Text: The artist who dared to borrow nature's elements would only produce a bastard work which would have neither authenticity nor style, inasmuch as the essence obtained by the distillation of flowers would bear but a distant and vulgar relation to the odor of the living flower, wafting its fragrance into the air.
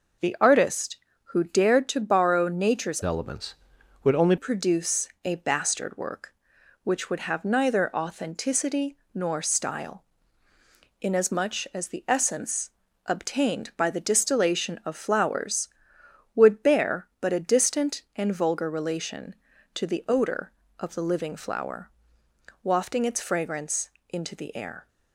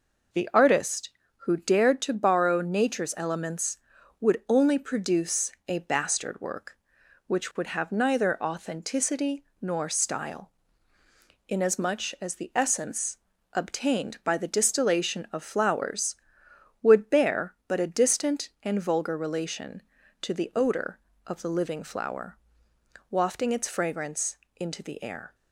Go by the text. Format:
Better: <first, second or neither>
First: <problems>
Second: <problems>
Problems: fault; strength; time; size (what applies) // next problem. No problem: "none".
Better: second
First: changes voice from "elements" to "only"; from 3.0 to 4.3 s; 1.3 s long // pauses between "produce" and "a"; slight; at 5.0 s; 0.16 s long // pauses between "authenticity" and "nor"; slight; at 8.9 s; 0.16 s long // pauses between "essence" and "obtained"; slight; at 12.6 s; 0.36 s long // pauses between "fragrance" and "into"; slight; at 23.8 s; 0.20 s long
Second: pauses between "produce" and "a"; slight; at 5.5 s; 0.16 s long // pauses between "authenticity" and "nor"; slight; at 9.4 s; 0.16 s long // pauses between "essence" and "obtained"; slight; at 13.1 s; 0.36 s long // pauses between "fragrance" and "into"; slight; at 24.3 s; 0.20 s long